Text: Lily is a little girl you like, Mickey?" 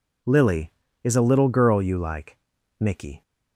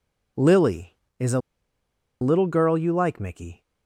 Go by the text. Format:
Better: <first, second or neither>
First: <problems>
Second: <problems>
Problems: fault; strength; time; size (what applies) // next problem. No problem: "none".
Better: first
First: none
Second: pauses between "a" and "little"; noticeable; at 1.3 s; 0.82 s long